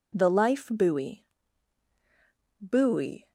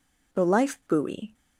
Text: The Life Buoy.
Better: second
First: says "Buoy" twice; at 2.5 s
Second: none

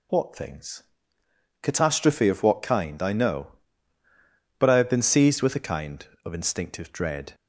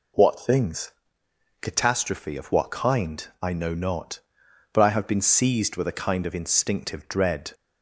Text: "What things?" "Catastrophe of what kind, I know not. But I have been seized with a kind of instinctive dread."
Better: second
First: skips "not"; at 4.0 s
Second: none

